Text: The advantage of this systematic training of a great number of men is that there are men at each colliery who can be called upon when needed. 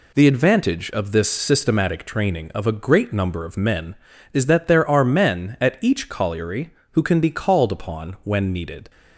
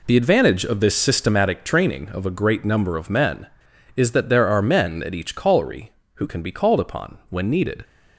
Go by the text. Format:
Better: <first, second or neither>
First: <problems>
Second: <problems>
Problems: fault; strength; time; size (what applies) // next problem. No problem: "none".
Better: neither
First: none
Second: none